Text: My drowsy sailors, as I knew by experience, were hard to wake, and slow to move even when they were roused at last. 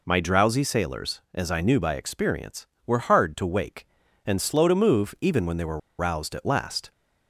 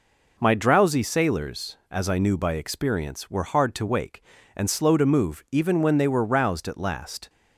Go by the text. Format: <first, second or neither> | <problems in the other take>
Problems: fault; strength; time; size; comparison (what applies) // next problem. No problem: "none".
second | pauses between "were" and "roused"; slight; at 5.7 s; 0.20 s long